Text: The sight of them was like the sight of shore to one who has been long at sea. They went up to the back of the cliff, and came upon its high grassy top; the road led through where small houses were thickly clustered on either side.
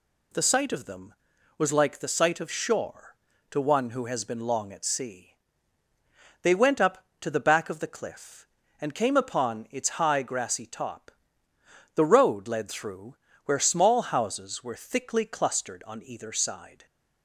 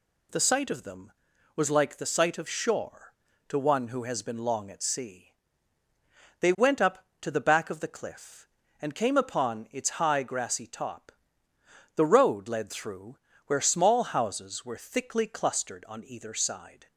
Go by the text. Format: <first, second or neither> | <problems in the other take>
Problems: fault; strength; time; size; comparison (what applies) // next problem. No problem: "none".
neither | pauses between "through" and "where"; slight; the same in both